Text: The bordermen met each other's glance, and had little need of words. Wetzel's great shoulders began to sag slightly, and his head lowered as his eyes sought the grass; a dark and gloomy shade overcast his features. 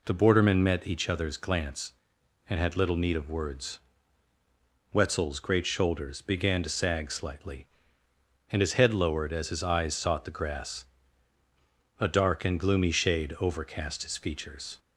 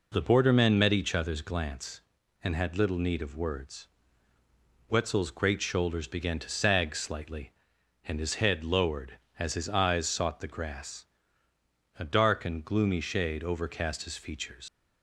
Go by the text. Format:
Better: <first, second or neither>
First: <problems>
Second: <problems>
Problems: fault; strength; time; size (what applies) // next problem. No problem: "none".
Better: first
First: none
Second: leaves "features" unfinished; at 14.6 s; 85 ms